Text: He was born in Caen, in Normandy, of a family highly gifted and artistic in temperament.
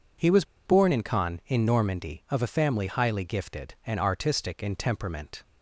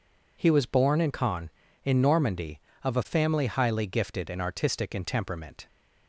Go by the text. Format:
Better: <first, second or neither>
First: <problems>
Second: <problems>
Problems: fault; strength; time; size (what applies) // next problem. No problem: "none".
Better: second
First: pauses between "was" and "born"; slight; at 0.4 s; 0.21 s long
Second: none